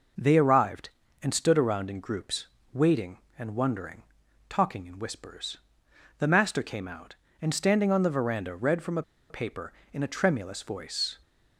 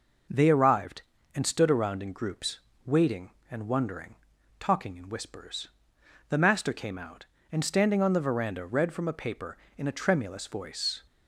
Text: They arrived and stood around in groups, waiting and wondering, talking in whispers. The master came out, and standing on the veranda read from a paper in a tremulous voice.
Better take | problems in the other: second | pauses between "a" and "paper"; slight; at 9.0 s; 0.27 s long

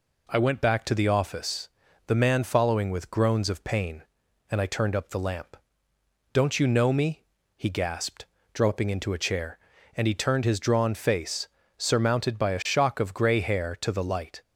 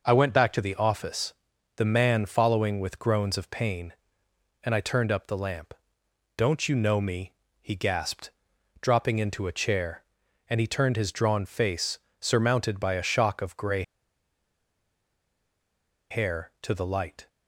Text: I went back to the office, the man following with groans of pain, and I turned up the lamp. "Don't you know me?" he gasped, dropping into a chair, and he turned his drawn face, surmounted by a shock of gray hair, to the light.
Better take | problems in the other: first | pauses between "gray" and "hair"; strong; at 13.8 s; 2.2 s long

